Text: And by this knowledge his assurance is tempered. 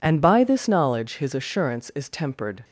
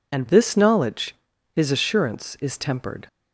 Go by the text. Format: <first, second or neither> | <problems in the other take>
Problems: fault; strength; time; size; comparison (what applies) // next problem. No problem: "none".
first | skips "by"; at 0.2 s // pauses between "knowledge" and "his"; at 1.1 s; 0.38 s long